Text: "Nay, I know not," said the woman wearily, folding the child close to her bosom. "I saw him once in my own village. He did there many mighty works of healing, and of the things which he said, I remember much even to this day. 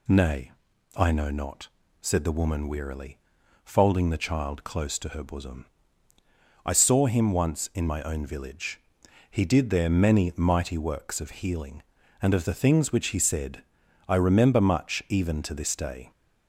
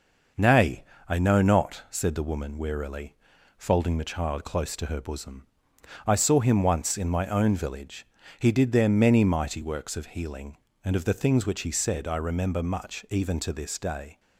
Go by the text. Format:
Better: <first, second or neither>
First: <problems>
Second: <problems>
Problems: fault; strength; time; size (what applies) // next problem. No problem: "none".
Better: neither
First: none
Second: none